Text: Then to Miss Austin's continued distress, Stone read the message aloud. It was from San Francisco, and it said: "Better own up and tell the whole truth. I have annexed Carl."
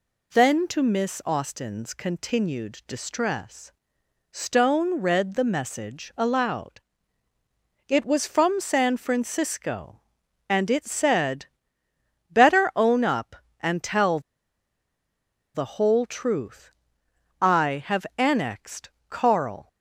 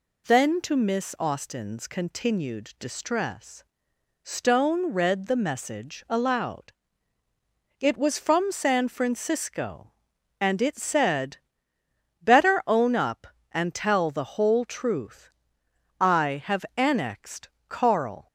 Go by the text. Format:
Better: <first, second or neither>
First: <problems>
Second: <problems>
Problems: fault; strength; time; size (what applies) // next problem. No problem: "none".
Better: second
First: pauses between "tell" and "the"; strong; at 14.1 s; 1.3 s long // pauses between "annexed" and "Carl"; slight; at 18.8 s; 0.20 s long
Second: pauses between "annexed" and "Carl"; slight; at 17.4 s; 0.20 s long